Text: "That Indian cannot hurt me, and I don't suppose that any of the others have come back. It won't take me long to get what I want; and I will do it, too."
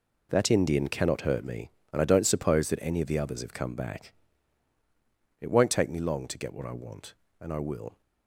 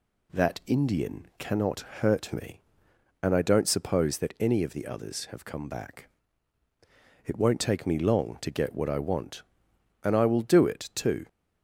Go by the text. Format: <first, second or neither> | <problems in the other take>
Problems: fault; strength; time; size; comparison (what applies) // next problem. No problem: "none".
second | stops before "do it too"; at 8.0 s